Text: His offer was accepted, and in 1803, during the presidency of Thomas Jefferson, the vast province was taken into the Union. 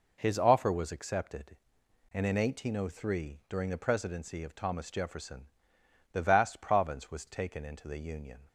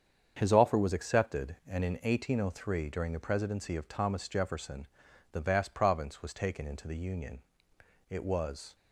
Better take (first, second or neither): first